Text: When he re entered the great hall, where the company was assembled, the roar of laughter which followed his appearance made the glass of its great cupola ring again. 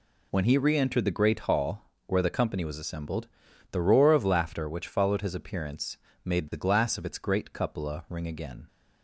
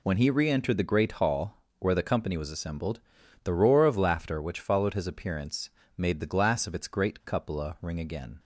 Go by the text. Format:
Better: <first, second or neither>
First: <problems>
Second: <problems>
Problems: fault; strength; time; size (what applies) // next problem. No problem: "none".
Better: neither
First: pauses between "appearance" and "made"; slight; at 5.9 s; 0.28 s long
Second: pauses between "appearance" and "made"; slight; at 5.6 s; 0.28 s long